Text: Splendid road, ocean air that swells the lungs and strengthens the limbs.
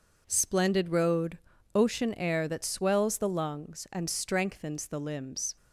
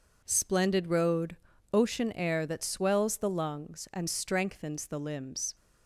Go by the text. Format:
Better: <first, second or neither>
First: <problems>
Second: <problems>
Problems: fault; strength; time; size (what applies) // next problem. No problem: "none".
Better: neither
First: none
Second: none